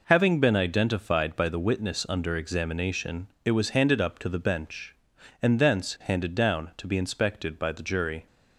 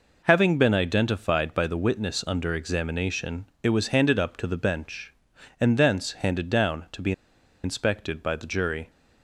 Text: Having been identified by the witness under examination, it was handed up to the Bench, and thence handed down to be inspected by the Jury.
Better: first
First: none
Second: pauses between "be" and "inspected"; noticeable; at 7.1 s; 0.51 s long

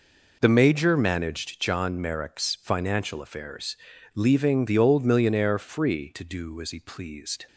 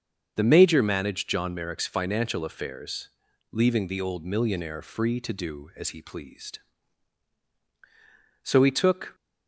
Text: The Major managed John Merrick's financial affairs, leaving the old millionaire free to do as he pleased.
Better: first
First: none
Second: starts louder than the rest; until 1.3 s; 7 dB // goes on to say "So he took"; noticeable; from 8.4 s on; 0.72 s long

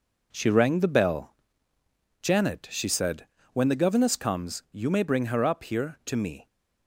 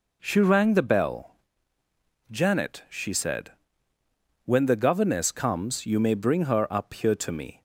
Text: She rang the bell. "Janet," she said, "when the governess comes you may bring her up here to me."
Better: second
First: gets quieter; strong; throughout; 8 dB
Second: none

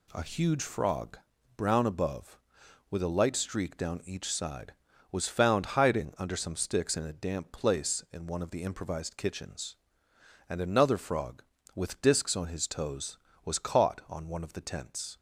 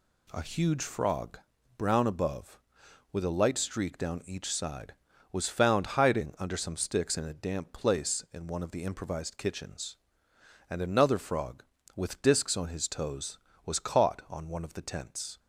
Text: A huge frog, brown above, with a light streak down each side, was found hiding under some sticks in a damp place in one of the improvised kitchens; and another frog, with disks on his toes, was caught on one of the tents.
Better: neither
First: none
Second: none

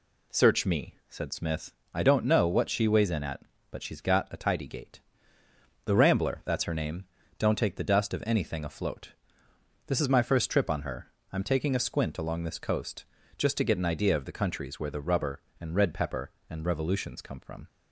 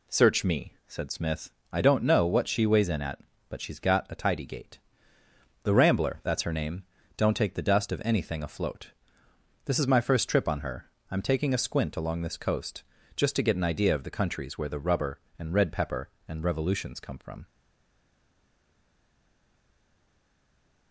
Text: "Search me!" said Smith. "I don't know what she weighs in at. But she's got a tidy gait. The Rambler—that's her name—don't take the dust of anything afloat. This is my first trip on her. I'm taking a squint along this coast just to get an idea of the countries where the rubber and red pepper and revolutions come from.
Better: first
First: pauses between "coast" and "just"; slight; at 13.0 s; 0.34 s long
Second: pauses between "coast" and "just"; slight; at 12.8 s; 0.34 s long // stays silent after the last word; strong; from 17.4 s on; 3.5 s long

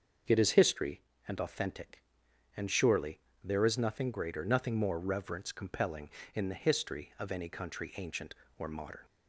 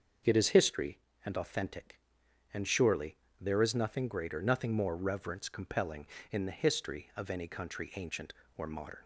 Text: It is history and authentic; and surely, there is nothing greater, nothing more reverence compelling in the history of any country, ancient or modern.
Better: neither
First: starts louder than the rest; until 1.5 s; 6.5 dB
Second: starts louder than the rest; until 1.5 s; 6.5 dB

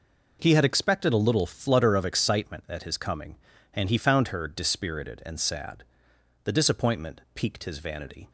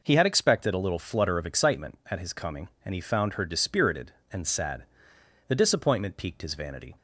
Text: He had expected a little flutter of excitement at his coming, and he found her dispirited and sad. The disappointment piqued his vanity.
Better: neither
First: none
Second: none

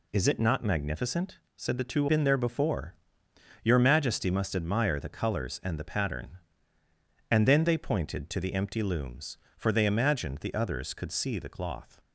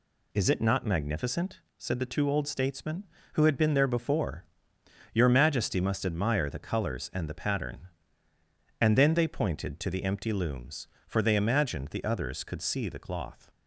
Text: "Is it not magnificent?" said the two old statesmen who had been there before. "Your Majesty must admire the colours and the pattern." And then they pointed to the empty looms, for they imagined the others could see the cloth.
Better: second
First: skips "old statesmen who had"; at 2.0 s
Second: none

